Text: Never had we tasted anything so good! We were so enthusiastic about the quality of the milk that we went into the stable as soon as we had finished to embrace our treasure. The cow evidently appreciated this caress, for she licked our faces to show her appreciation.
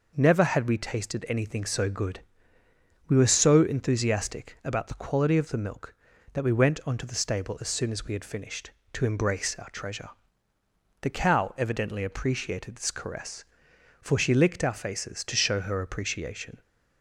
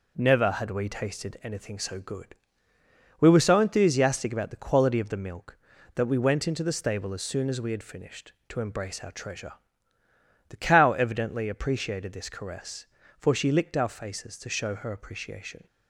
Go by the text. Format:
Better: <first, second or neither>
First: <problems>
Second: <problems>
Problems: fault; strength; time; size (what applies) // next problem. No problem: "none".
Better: second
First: says "onto" for "into"; at 6.8 s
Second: none